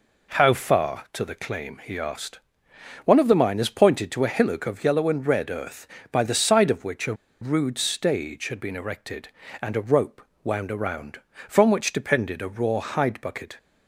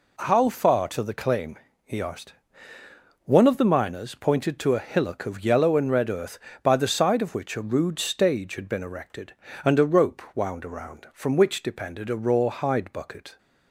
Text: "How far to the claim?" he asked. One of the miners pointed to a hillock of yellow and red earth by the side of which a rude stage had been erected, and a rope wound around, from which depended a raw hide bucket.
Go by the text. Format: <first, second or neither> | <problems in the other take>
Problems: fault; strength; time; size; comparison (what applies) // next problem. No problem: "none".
second | pauses between "a" and "rude"; slight; at 7.1 s; 0.26 s long // pauses between "rope" and "wound"; slight; at 10.2 s; 0.22 s long